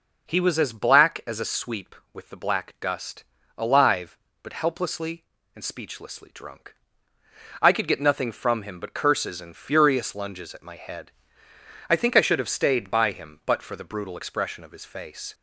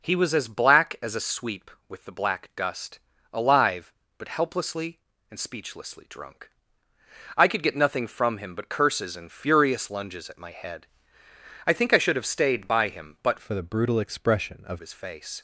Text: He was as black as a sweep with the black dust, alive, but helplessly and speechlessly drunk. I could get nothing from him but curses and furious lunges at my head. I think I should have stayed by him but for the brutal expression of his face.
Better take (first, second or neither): first